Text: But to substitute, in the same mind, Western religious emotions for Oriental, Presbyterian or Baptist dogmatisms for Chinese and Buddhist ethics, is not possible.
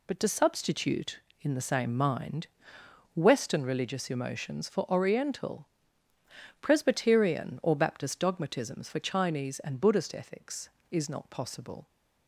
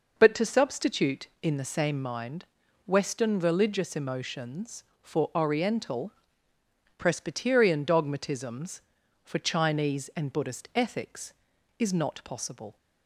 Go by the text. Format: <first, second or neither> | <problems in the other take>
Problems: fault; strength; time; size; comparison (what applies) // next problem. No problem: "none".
first | skips "or Baptist"; at 7.8 s